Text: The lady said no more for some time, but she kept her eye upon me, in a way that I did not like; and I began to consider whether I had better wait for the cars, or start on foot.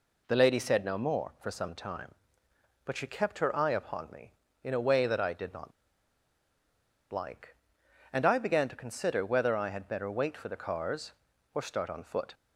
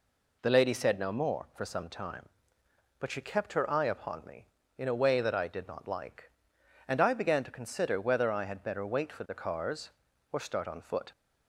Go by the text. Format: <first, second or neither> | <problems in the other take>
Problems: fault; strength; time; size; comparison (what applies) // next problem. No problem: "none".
second | pauses between "not" and "like"; strong; at 5.7 s; 1.4 s long